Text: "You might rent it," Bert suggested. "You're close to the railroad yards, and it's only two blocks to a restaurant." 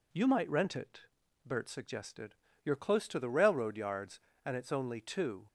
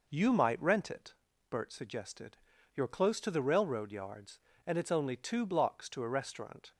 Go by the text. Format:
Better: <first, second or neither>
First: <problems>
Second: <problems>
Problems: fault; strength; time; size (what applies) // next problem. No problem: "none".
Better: second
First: stops before "blocks to a restaurant"; at 5.4 s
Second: none